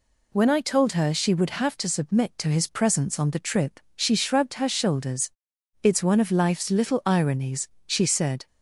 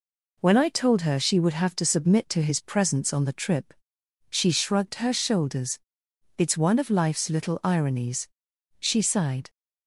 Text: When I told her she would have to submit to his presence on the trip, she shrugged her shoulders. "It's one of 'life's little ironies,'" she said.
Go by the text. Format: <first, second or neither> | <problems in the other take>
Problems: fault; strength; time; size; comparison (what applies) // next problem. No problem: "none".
first | says "sighed" for "said"; at 9.0 s